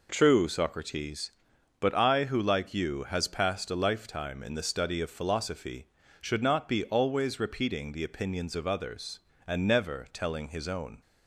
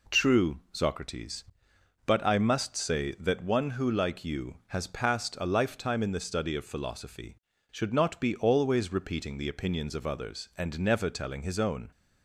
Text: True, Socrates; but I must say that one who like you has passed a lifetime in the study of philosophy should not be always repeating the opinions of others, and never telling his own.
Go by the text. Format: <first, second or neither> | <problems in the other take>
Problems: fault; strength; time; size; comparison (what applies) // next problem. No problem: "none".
second | skips "must say that one"; at 2.2 s